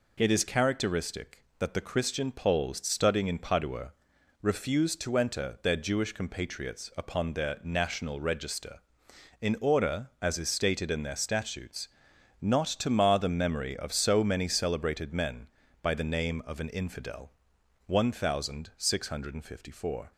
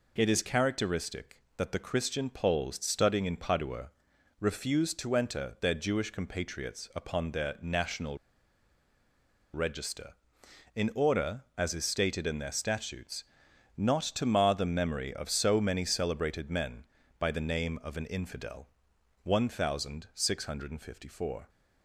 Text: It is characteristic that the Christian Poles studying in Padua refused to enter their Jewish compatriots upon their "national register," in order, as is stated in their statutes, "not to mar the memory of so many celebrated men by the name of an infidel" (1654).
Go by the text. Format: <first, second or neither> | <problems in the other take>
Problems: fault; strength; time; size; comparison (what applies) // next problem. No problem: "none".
first | pauses between "Padua" and "refused"; noticeable; at 3.9 s; 0.50 s long; noticeable in the first // pauses between "national" and "register"; strong; at 8.1 s; 1.3 s long